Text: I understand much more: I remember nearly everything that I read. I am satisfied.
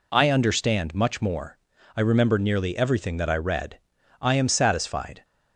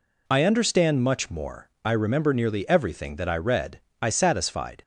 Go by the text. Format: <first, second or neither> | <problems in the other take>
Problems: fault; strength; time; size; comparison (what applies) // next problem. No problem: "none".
first | skips "am"; at 4.0 s